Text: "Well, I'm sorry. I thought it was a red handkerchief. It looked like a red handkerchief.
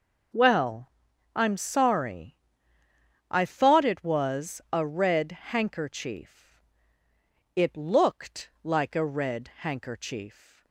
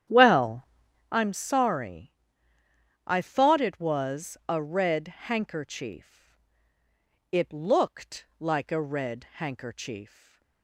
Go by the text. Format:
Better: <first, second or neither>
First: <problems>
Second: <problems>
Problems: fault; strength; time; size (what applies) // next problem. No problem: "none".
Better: first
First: none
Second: starts louder than the rest; strong; until 1.3 s; 10 dB // stays silent after the last word; slight; from 10.0 s on; 0.6 s long